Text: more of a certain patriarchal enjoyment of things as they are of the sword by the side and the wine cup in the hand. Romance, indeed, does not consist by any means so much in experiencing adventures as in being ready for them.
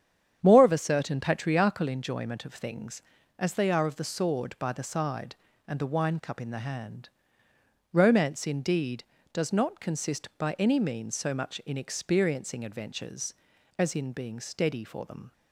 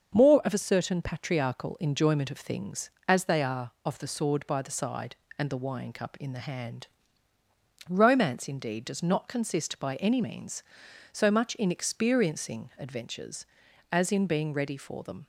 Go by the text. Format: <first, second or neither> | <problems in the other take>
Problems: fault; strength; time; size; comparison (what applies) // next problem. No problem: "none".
second | starts louder than the rest; strong; until 1.4 s; 8.5 dB; also in the second // says "steady" for "ready"; at 14.3 s